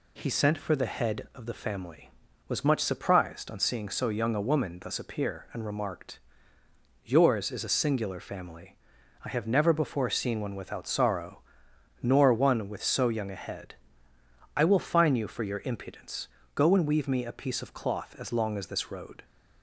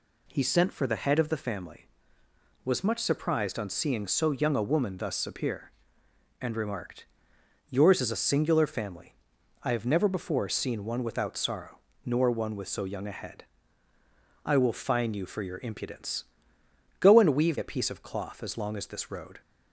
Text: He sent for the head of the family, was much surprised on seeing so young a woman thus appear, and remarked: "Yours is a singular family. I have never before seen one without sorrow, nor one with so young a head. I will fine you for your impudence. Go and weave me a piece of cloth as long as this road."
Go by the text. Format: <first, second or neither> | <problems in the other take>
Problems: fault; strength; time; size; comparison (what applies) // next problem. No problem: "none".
first | skips "me"; at 17.5 s